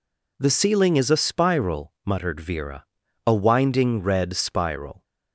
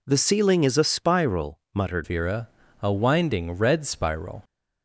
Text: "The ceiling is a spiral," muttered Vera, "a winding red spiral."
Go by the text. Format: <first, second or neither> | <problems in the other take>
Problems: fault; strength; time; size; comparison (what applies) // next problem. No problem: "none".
first | changes voice at "Vera"; from 2.0 s on; 2.4 s long